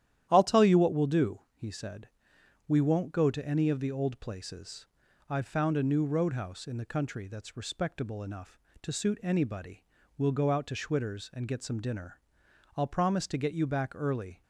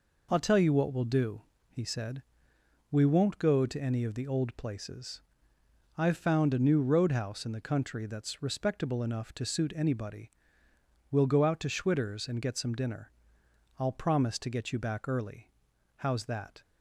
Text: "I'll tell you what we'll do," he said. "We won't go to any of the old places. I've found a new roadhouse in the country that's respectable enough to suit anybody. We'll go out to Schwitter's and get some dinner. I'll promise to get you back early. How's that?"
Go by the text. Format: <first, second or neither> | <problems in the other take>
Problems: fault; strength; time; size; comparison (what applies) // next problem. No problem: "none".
second | starts louder than the rest; strong; until 1.3 s; 11.5 dB // stops before "How's that"; at 14.4 s